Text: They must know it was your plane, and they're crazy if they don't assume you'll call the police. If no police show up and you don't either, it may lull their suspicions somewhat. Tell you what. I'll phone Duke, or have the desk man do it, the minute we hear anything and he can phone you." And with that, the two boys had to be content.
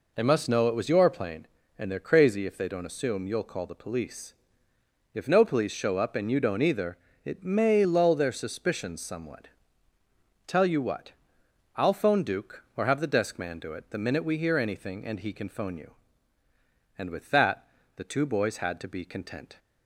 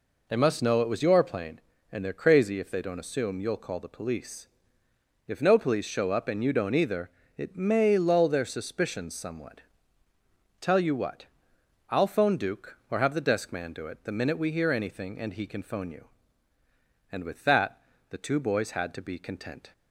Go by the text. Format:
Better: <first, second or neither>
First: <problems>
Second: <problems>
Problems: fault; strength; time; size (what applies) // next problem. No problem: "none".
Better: neither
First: none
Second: none